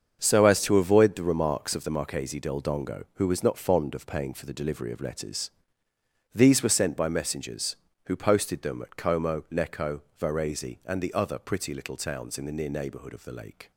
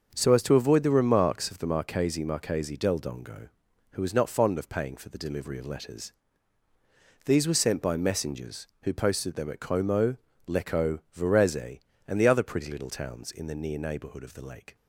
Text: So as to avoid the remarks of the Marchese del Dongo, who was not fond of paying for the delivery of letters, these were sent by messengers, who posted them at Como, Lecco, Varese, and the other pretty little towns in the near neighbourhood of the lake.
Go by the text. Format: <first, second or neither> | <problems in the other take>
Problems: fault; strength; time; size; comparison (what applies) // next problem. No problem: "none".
first | starts louder than the rest; until 1.1 s; 6.5 dB; also in the first // says "Marchese" twice; at 2.2 s